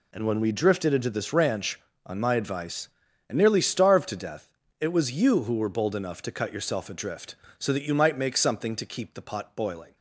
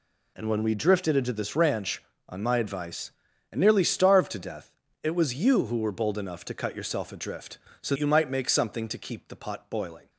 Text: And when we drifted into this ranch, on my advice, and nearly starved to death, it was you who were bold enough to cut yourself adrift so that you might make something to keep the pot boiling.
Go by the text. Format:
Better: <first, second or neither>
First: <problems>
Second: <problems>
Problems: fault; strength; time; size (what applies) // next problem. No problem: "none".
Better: first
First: none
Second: skips "that"; at 7.9 s